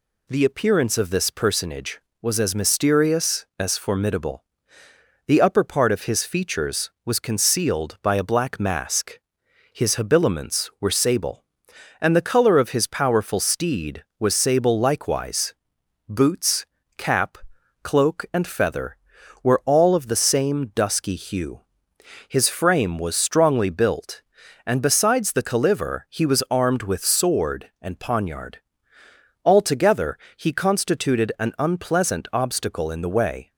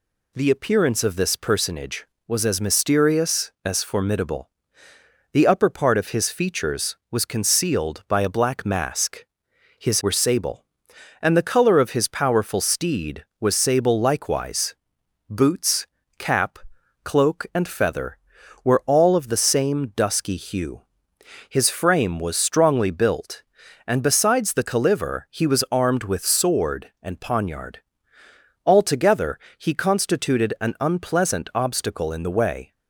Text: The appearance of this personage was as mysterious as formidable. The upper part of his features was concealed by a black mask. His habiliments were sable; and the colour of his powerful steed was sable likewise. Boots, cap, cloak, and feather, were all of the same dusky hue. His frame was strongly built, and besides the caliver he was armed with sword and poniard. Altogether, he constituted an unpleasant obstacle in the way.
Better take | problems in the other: first | skips "habiliments"; at 10.0 s

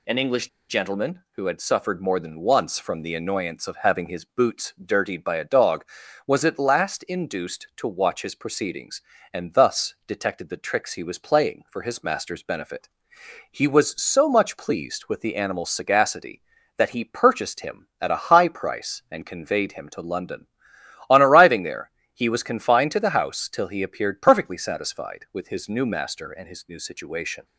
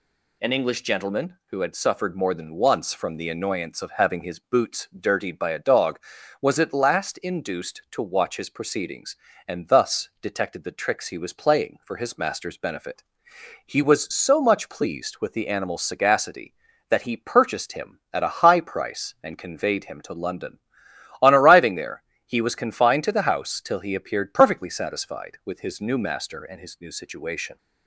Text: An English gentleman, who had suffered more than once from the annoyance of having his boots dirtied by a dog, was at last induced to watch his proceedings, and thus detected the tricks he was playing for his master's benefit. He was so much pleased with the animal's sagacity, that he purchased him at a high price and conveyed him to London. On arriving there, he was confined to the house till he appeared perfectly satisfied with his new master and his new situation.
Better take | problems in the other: second | pauses between "English" and "gentleman"; slight; at 0.4 s; 0.21 s long

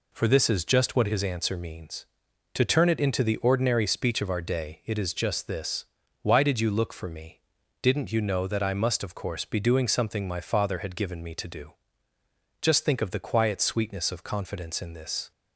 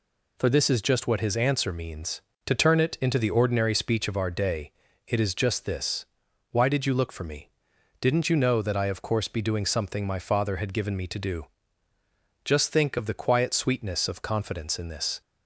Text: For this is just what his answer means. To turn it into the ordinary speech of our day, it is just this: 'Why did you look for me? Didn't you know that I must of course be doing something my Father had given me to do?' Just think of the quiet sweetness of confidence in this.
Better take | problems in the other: first | skips "must"; at 8.8 s

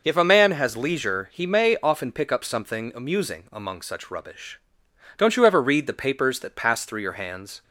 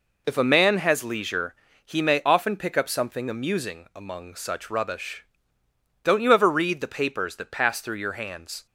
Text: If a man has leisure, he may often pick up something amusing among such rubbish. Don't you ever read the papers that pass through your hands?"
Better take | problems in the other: neither | none

